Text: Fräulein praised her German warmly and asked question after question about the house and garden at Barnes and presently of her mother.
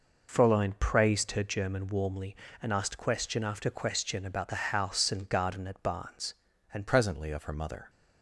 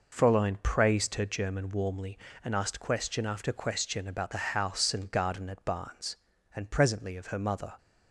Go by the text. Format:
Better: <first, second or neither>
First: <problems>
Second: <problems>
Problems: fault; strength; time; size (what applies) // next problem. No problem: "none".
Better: second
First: changes voice at "presently"; from 6.8 s on; 1.0 s long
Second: none